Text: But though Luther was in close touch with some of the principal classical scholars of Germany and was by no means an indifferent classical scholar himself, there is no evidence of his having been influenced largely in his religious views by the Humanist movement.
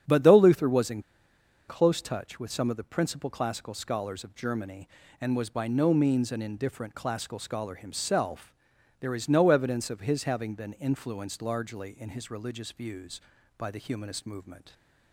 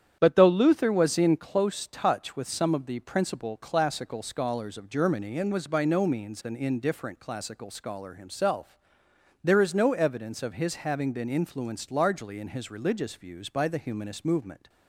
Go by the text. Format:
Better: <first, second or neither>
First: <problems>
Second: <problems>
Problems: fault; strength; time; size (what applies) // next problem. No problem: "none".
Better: second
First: starts louder than the rest; strong; until 1.7 s; 8.5 dB // pauses between "in" and "close"; noticeable; at 1.0 s; 0.66 s long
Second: starts louder than the rest; strong; until 1.2 s; 9.5 dB